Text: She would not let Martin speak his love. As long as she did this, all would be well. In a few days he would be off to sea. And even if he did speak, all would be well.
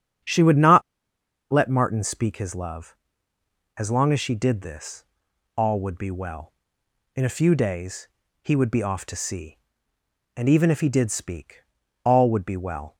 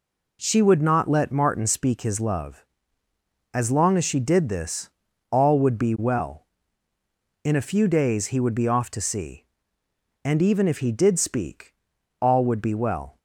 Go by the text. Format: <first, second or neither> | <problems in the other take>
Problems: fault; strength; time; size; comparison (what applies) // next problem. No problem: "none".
second | starts louder than the rest; strong; until 1.9 s; 8.5 dB // pauses between "not" and "let"; noticeable; at 0.8 s; 0.71 s long // pauses between "days" and "he"; slight; at 8.0 s; 0.36 s long